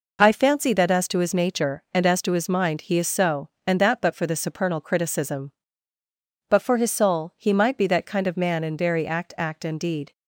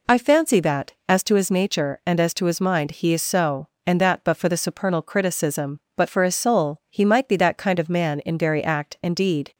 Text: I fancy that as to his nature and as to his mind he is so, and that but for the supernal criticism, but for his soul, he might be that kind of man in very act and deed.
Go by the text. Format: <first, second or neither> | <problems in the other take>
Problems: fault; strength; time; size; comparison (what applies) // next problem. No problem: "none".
second | says "act" twice; at 9.3 s